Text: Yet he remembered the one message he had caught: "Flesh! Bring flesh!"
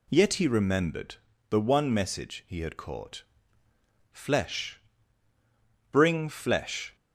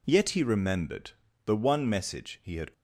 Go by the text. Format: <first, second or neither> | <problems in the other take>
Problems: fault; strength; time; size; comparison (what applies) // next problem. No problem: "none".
first | pauses between "remembered" and "the"; slight; at 1.1 s; 0.36 s long; slight in the first // stops before "caught Flesh Bring flesh"; at 2.7 s